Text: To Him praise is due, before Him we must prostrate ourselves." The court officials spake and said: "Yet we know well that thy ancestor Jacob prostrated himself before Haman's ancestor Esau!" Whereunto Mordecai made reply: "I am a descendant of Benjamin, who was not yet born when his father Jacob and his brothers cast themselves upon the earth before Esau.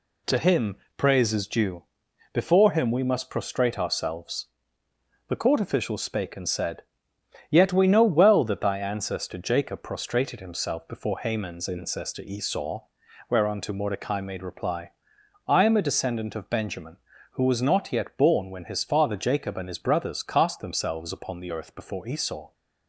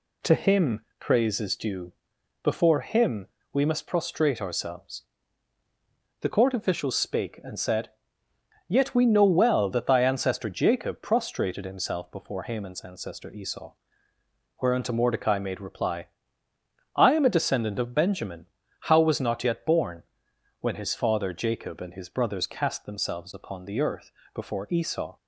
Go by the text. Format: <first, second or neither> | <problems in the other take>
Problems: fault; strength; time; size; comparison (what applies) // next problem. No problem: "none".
first | pauses between "Him" and "praise"; slight; at 0.8 s; 0.18 s long; slight in the first // pauses between "Him" and "we"; slight; at 3.2 s; 0.26 s long // says "how" for "who"; at 18.8 s // pauses between "born" and "when"; noticeable; at 20.0 s; 0.56 s long // pauses between "earth" and "before"; slight; at 24.1 s; 0.22 s long